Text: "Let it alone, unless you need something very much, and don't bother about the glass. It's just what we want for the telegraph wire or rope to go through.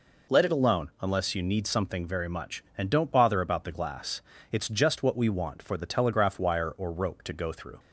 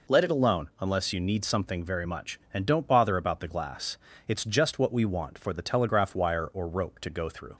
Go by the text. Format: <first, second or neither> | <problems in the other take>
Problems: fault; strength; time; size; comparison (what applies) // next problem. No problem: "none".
neither | none